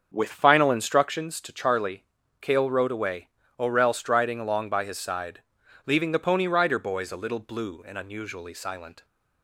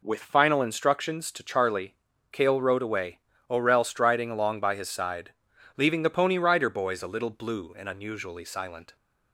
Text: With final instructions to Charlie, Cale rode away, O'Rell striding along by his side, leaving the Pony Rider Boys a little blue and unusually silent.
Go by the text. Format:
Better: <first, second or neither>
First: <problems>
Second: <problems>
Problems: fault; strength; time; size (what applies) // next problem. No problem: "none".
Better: second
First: starts louder than the rest; strong; until 1.2 s; 7 dB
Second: none